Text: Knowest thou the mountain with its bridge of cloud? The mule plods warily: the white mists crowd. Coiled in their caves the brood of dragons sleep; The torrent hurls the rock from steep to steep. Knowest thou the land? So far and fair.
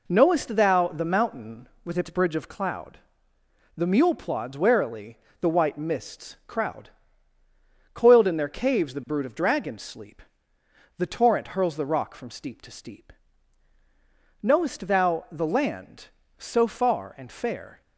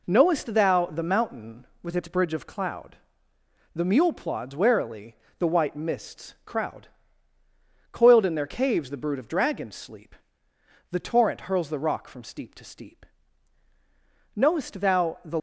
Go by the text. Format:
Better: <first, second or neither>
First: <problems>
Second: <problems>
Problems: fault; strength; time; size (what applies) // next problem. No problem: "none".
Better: first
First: none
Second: stops before "land So far and fair"; at 15.3 s